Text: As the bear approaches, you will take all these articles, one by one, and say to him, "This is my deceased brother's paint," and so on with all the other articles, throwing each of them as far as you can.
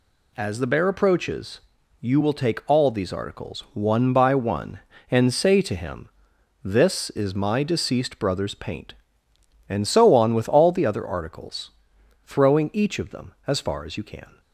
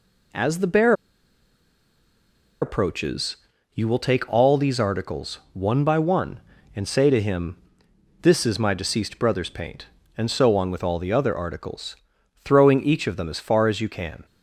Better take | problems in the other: first | pauses between "bear" and "approaches"; strong; at 0.9 s; 1.6 s long

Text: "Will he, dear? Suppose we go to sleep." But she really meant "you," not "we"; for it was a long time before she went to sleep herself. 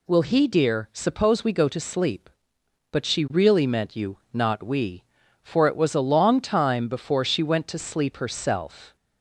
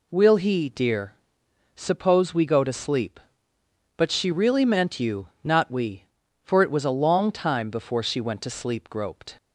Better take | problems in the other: first | says "groped" for "herself"; at 8.8 s

